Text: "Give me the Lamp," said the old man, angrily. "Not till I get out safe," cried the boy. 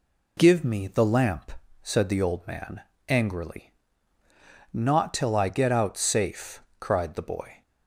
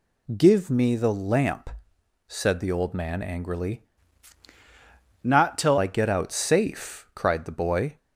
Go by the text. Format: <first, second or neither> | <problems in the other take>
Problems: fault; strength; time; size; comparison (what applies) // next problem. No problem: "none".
first | changes voice from "Not" to "till"; from 5.2 to 5.7 s; 0.5 s long